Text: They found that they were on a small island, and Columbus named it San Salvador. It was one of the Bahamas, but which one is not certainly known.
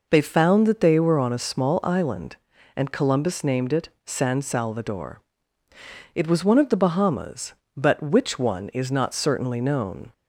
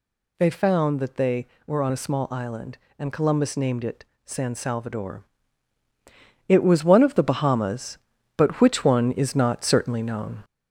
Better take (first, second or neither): first